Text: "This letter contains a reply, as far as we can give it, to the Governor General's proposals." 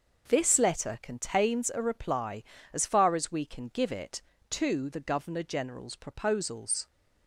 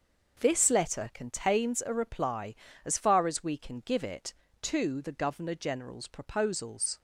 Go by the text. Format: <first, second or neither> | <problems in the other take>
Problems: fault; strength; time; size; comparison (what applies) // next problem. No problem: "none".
neither | starts louder than the rest; the same in both